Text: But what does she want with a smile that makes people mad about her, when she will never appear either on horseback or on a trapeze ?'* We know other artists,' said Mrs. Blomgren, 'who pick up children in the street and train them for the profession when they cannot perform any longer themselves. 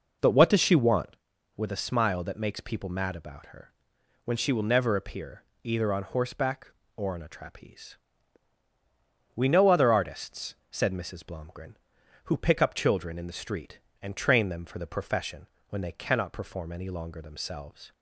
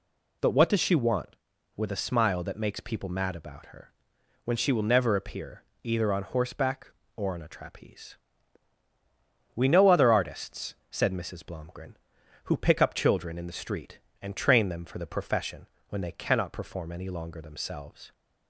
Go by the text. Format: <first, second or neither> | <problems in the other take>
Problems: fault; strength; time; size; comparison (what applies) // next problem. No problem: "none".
second | starts louder than the rest; strong; until 1.3 s; 7.5 dB // pauses between "appear" and "either"; slight; at 5.4 s; 0.22 s long; slight in the second // pauses between "profession" and "when"; slight; at 15.4 s; 0.24 s long; slight in the second